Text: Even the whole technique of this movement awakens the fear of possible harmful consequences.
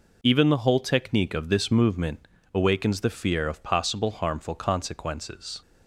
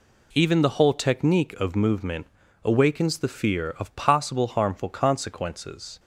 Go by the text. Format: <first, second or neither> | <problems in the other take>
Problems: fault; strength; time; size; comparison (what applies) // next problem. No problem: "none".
first | skips "this"; at 1.7 s // pauses between "movement" and "awakens"; at 2.2 s; 0.38 s long; slight in the first